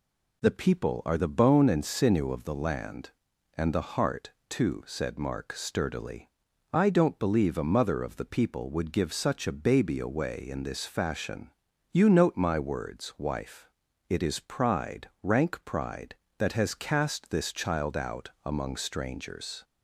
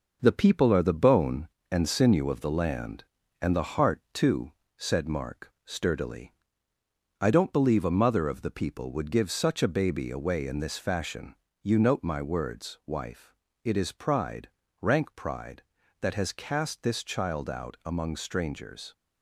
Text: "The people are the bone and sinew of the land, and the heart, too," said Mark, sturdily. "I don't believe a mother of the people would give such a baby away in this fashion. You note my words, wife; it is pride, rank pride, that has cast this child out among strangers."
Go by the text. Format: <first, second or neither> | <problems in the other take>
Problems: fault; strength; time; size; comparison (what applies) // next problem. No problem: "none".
first | gets quieter; noticeable; throughout; 5 dB